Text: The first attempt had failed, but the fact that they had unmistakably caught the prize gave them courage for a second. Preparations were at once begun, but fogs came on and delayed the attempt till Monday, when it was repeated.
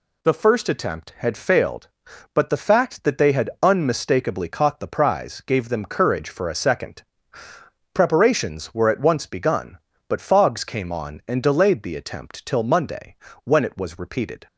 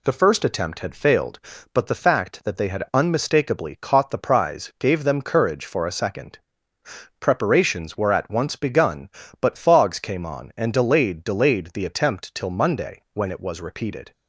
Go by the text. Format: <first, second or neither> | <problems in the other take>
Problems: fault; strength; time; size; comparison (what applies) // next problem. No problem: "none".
first | says "delayed" twice; at 11.2 s